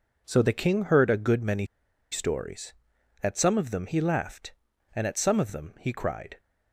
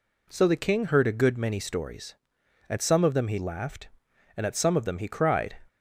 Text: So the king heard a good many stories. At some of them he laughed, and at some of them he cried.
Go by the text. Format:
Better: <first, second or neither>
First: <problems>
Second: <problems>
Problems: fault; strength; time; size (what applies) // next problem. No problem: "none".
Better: second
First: pauses between "many" and "stories"; at 1.6 s; 0.45 s long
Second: none